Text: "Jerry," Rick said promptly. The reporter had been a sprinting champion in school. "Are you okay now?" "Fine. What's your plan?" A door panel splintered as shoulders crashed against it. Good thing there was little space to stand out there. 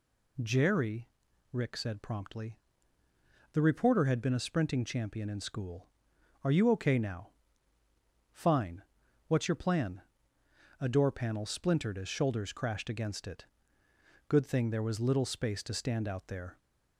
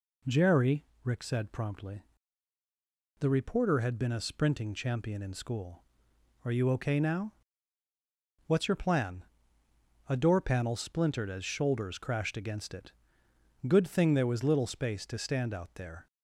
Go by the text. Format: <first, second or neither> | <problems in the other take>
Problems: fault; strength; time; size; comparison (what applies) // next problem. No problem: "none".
first | skips "Fine"; at 7.8 s